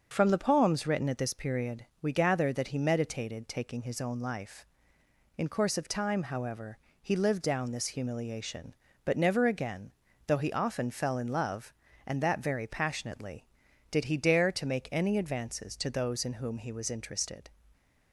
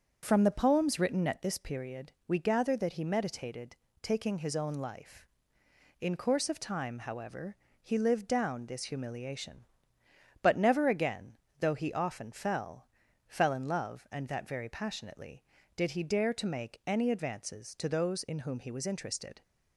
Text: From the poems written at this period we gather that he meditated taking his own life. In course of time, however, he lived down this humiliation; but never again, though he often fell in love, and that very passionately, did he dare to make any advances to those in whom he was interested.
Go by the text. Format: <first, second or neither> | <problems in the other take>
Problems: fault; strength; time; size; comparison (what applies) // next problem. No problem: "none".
first | starts louder than the rest; until 1.2 s; 7 dB; also in the first // pauses between "period" and "we"; slight; at 2.0 s; 0.18 s long; slight in the first // pauses between "meditated" and "taking"; slight; at 3.7 s; 0.24 s long // says "fell" twice; at 13.2 s